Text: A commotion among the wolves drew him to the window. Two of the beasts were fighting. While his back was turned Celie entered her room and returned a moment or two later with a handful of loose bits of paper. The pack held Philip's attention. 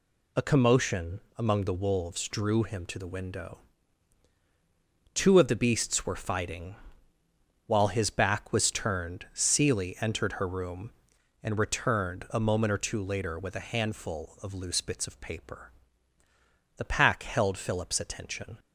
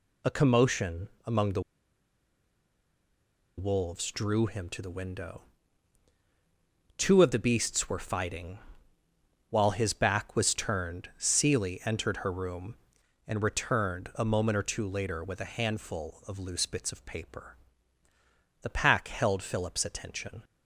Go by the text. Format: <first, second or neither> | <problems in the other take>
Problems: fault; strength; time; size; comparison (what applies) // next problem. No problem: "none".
first | pauses between "commotion" and "among"; slight; at 1.0 s; 0.18 s long; slight in the first // pauses between "the" and "wolves"; strong; at 1.6 s; 1.9 s long